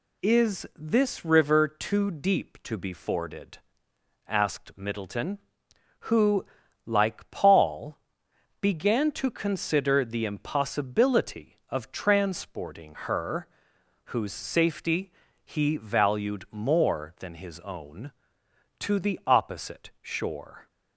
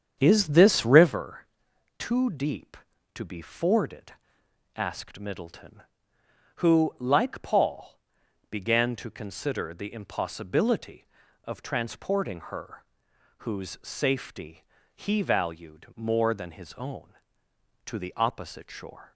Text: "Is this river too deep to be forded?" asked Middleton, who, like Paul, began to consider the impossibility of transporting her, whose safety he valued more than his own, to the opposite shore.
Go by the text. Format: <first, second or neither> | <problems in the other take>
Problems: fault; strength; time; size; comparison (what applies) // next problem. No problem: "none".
first | starts louder than the rest; strong; until 1.2 s; 8 dB // pauses between "river" and "too"; noticeable; at 1.4 s; 0.52 s long // pauses between "safety" and "he"; slight; at 14.6 s; 0.30 s long; slight in the first